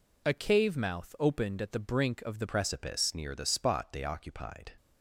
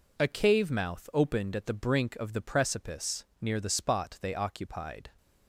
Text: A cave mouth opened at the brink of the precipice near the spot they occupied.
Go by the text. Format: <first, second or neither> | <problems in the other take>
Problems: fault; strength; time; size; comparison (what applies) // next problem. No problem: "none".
second | changes voice at "precipice"; from 2.4 s on; 2.3 s long